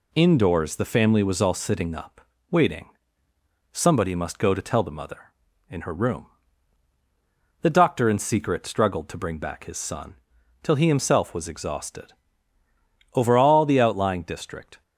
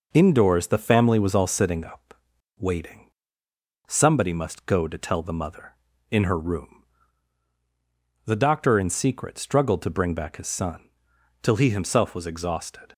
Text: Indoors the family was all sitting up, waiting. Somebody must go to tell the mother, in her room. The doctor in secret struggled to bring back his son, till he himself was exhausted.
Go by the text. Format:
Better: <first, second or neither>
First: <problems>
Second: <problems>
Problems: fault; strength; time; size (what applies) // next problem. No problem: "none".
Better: second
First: goes on to say "Over all the outlying district"; strong; from 13.1 s on; 1.6 s long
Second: none